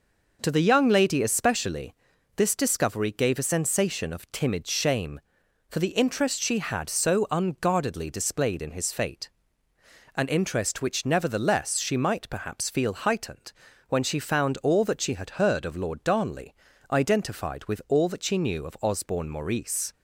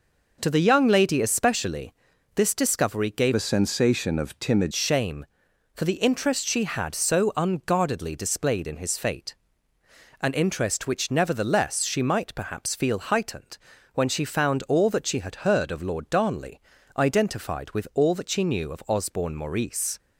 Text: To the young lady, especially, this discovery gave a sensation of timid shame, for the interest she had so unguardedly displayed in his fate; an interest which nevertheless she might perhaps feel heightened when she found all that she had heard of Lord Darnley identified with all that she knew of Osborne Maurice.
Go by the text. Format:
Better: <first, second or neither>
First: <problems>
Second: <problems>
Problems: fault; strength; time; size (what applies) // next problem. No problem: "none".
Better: first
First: pauses between "heightened" and "when"; at 13.5 s; 0.38 s long // pauses between "Darnley" and "identified"; at 16.5 s; 0.38 s long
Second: changes voice from "a" to "timid"; from 3.3 to 4.7 s; 1.4 s long // pauses between "heightened" and "when"; at 13.5 s; 0.38 s long // pauses between "Darnley" and "identified"; at 16.5 s; 0.38 s long